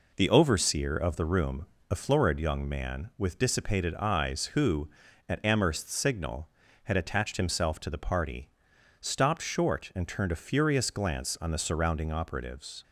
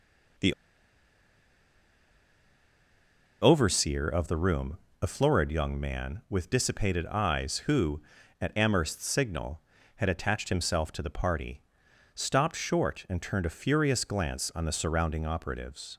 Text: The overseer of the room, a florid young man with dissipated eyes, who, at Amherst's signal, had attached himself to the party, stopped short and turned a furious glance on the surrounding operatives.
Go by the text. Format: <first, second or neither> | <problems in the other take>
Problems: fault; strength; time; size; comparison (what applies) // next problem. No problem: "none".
first | pauses between "The" and "overseer"; strong; at 0.5 s; 2.8 s long